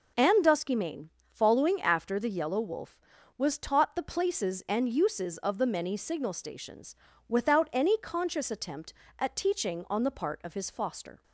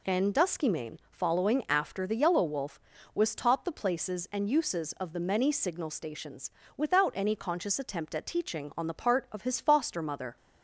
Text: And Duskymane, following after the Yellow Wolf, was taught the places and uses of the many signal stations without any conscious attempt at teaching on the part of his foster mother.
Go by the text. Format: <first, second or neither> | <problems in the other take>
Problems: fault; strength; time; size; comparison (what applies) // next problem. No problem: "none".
second | pauses between "stations" and "without"; slight; at 6.9 s; 0.32 s long; slight in the second // stops before "mother"; at 11.2 s